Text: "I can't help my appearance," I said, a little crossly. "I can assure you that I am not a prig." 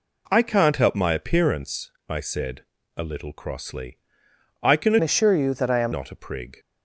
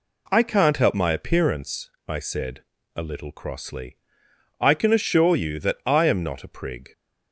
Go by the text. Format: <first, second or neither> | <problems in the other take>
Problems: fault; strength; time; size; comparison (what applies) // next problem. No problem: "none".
second | changes voice from "assure" to "am"; from 5.0 to 5.9 s; 0.9 s long